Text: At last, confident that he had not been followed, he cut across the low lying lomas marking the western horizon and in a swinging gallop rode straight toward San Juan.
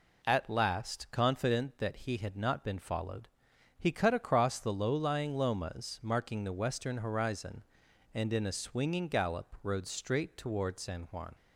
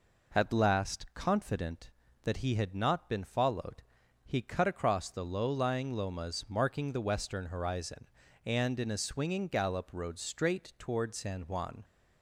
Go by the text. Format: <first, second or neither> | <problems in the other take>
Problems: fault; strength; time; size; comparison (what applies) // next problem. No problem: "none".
neither | none